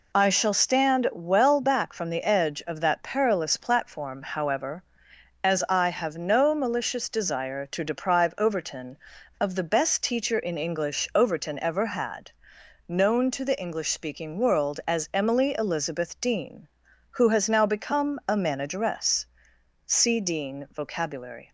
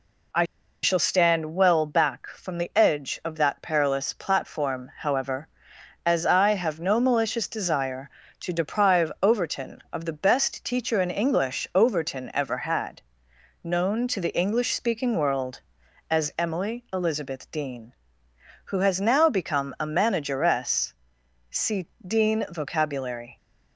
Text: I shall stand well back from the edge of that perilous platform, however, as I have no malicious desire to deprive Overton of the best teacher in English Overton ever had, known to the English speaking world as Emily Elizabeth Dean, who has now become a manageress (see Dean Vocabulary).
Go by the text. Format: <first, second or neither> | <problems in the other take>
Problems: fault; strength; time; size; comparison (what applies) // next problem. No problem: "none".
first | pauses between "I" and "shall"; at 0.4 s; 0.37 s long // pauses between "see" and "Dean"; slight; at 21.8 s; 0.20 s long